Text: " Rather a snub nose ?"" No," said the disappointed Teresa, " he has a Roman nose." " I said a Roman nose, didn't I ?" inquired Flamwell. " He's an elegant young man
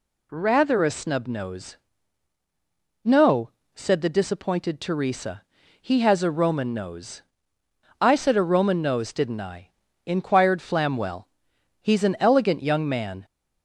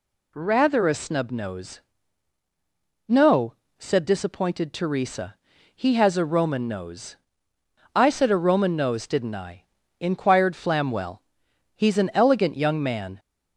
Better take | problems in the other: first | skips "the"; at 4.0 s

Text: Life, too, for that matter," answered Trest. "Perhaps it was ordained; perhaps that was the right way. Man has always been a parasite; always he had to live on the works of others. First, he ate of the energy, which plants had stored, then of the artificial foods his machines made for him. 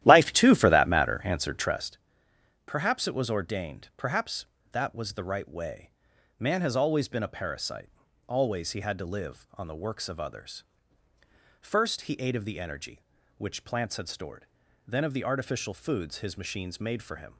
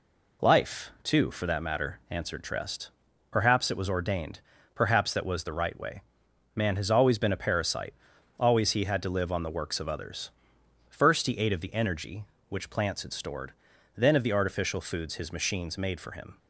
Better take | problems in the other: second | starts louder than the rest; strong; until 1.9 s; 13 dB

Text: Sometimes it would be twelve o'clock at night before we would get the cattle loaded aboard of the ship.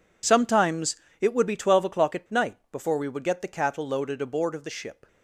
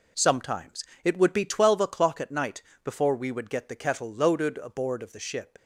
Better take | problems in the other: first | pauses between "Sometimes" and "it"; slight; at 0.8 s; 0.18 s long; slight in the first // pauses between "night" and "before"; slight; at 2.6 s; 0.22 s long; slight in the first // says "kettle" for "cattle"; at 3.7 s

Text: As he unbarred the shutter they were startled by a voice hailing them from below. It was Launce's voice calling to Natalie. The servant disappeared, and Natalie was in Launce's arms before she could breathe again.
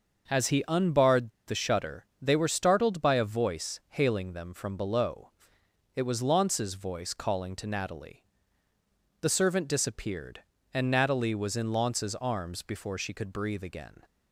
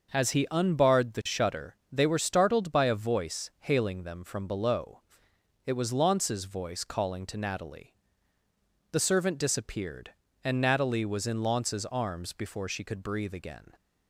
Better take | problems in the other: second | starts louder than the rest; noticeable; until 1.4 s; 6 dB; noticeable in the second // pauses between "unbarred" and "the"; slight; at 1.2 s; 0.17 s long

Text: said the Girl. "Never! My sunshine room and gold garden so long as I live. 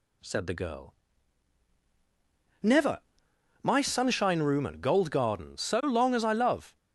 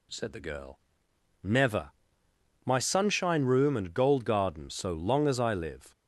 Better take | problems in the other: second | says "love" for "live"; at 6.3 s

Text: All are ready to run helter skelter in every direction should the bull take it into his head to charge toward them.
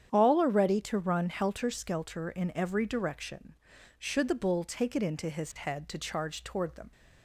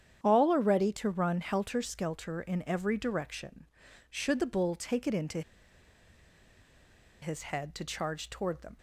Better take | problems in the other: first | starts louder than the rest; strong; until 1.2 s; 9 dB; strong in the first // pauses between "into" and "his"; strong; at 5.4 s; 1.8 s long

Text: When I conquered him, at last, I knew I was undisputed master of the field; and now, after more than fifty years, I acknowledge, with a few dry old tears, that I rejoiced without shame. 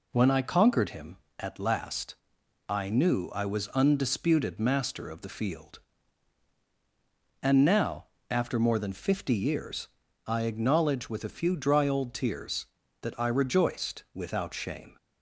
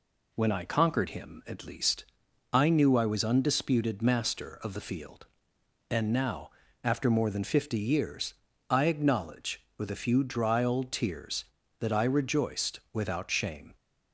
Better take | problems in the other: first | says "least" for "last"; at 1.6 s

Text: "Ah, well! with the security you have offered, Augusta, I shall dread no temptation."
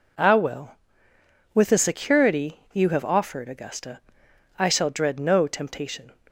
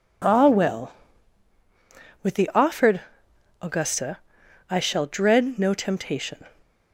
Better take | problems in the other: first | skips "security you have"; at 2.5 s

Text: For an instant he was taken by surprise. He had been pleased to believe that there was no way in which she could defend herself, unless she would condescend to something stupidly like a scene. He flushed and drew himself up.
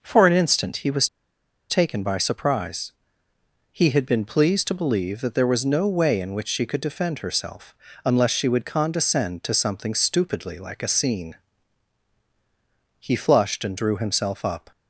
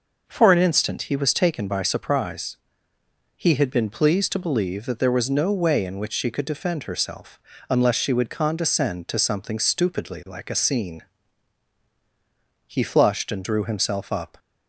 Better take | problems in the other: second | pauses between "was" and "taken"; noticeable; at 1.0 s; 0.63 s long

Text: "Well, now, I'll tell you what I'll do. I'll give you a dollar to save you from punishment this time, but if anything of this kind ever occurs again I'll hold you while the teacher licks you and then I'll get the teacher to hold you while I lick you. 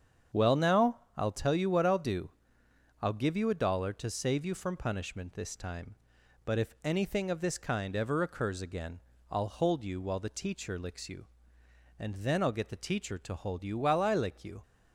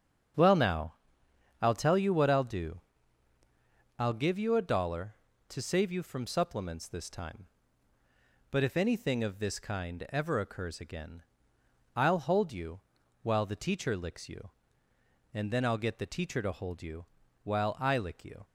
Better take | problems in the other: first | starts louder than the rest; strong; until 2.0 s; 7.5 dB; strong in the first // says "supplements" for "punishment"; at 6.2 s // pauses between "again" and "I'll"; noticeable; at 11.2 s; 0.74 s long; slight in the first // pauses between "you" and "while"; at 12.8 s; 0.40 s long // pauses between "you" and "while"; at 17.0 s; 0.38 s long

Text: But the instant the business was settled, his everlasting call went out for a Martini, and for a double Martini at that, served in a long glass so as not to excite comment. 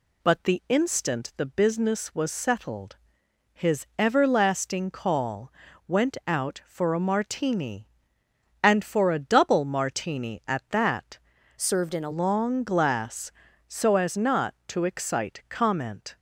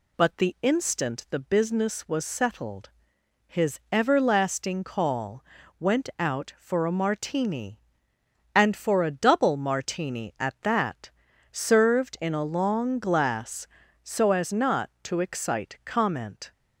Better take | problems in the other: second | pauses between "call" and "went"; slight; at 5.5 s; 0.36 s long; slight in the second // changes voice from "served" to "a"; from 11.5 to 12.1 s; 0.6 s long

